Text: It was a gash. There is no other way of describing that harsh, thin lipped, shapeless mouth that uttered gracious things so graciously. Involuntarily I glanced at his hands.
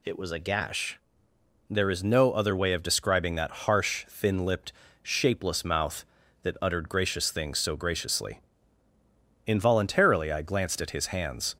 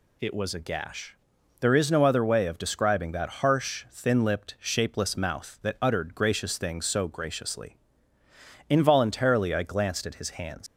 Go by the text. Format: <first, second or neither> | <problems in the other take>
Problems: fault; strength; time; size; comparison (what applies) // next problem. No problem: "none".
first | leaves "hands" unfinished; at 10.6 s; 135 ms